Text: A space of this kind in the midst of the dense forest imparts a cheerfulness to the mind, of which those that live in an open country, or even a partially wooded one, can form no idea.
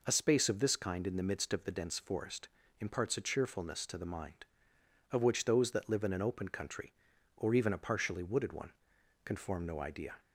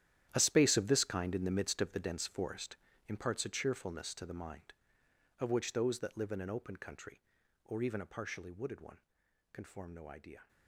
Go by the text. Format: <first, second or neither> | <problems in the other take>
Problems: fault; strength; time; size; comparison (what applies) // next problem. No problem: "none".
first | gets quieter; strong; throughout; 14 dB // pauses between "forest" and "imparts"; slight; at 2.7 s; 0.30 s long; slight in the first